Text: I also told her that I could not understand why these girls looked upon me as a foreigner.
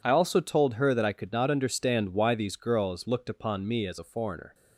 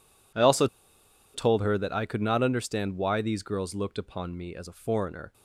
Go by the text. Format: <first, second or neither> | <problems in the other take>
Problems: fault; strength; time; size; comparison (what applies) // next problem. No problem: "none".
first | pauses between "also" and "told"; noticeable; at 0.6 s; 0.67 s long